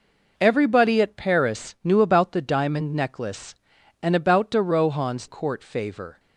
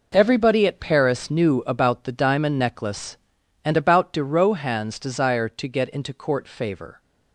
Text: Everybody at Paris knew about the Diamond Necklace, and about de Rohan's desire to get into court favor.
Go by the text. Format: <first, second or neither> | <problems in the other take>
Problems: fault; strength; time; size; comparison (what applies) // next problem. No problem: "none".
second | skips "desire to get into"; at 5.2 s